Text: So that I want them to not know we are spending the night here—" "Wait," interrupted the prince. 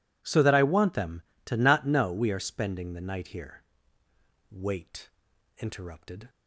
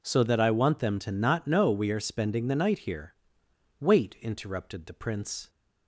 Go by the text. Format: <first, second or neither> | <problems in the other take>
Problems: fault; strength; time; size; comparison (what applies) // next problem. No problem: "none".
second | stops before "the prince"; at 6.2 s